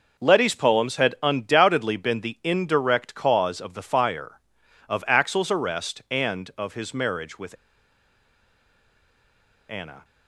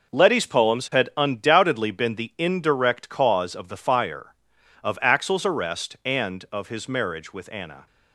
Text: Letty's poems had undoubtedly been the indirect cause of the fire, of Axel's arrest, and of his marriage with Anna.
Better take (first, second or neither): second